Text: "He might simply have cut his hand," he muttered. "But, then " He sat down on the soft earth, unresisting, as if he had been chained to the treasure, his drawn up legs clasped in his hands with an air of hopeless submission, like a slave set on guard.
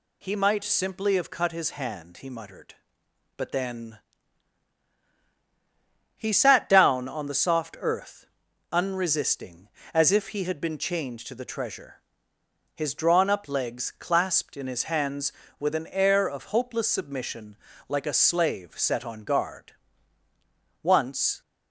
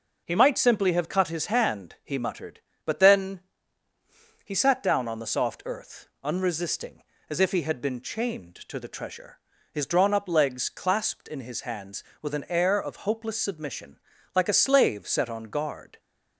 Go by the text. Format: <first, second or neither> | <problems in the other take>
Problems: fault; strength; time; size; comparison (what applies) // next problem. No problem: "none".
second | goes on to say "Once"; from 20.8 s on; 0.58 s long